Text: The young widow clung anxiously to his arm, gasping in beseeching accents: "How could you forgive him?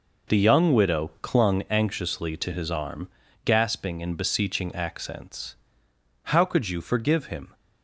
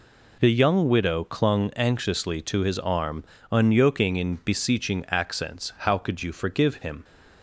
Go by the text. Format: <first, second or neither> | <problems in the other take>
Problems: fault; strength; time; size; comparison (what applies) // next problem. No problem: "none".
first | says "unyoking" for "gasping"; at 3.5 s